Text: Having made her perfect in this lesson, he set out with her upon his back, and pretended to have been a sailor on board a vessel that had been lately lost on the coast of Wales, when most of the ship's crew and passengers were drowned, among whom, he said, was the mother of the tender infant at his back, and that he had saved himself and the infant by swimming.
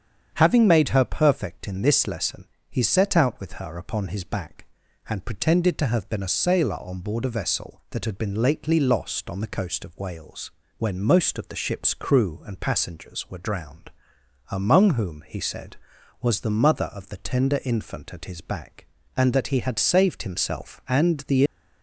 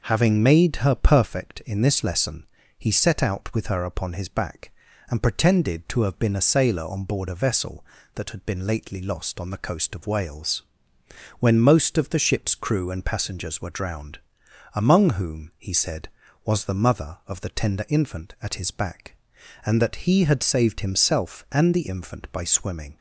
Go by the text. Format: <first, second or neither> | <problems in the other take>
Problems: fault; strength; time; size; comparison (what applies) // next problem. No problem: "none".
second | starts louder than the rest; strong; until 1.3 s; 8 dB // stops before "infant by swimming"; at 21.4 s